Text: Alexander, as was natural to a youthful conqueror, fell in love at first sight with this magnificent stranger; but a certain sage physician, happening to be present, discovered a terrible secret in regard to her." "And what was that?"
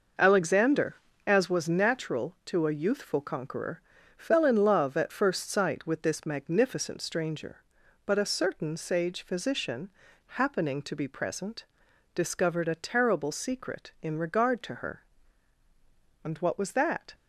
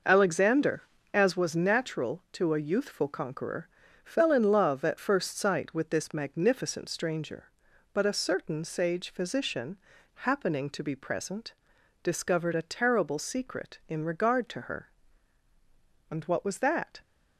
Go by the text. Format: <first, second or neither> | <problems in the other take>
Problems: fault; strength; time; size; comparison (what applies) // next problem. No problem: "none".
neither | none